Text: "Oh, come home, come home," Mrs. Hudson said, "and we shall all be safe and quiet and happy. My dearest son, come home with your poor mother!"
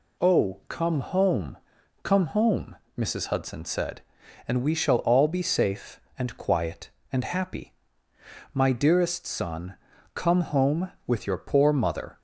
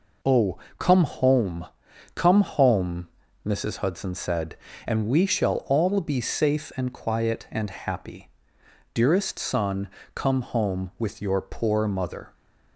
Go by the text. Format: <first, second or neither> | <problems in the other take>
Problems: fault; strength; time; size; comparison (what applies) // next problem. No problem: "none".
first | skips "My"; at 8.6 s